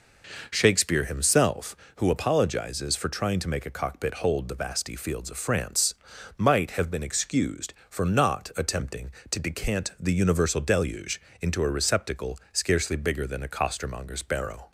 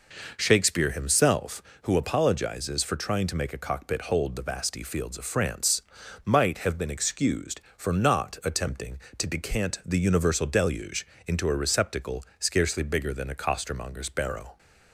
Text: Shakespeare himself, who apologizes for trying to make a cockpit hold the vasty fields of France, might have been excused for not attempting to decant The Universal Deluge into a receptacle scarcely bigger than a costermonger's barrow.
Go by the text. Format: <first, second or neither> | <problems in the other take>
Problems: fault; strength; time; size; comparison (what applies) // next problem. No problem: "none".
neither | pauses between "Deluge" and "into"; slight; the same in both